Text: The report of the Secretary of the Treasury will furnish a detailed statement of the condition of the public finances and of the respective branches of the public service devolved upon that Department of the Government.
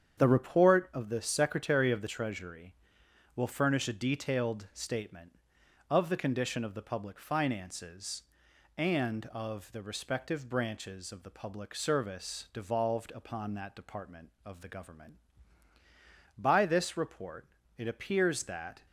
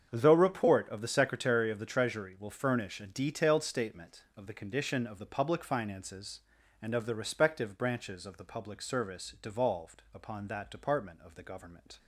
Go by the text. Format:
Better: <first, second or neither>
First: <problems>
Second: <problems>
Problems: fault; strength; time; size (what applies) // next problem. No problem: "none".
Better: second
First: starts louder than the rest; strong; until 1.2 s; 8 dB // goes on to say "By this report it appears that"; strong; from 16.3 s on; 2.4 s long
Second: starts louder than the rest; strong; until 1.1 s; 7.5 dB